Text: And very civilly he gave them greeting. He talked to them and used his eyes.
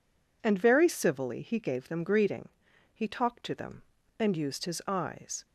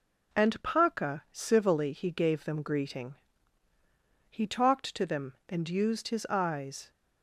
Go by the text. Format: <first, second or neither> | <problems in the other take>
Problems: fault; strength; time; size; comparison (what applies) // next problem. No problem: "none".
first | says "paca" for "very"; at 0.6 s